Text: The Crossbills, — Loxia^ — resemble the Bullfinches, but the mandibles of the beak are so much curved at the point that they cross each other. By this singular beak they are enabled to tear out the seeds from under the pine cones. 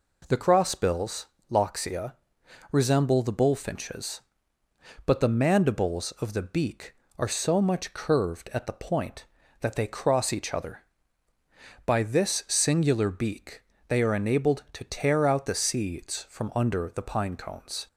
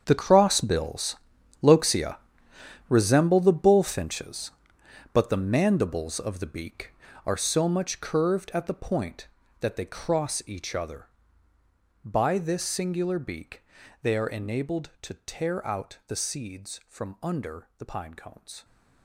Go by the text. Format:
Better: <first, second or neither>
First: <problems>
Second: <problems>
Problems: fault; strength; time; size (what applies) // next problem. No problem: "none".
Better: first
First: pauses between "beak" and "they"; slight; at 13.6 s; 0.26 s long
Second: gets quieter; strong; throughout; 15 dB // pauses between "beak" and "they"; at 13.6 s; 0.40 s long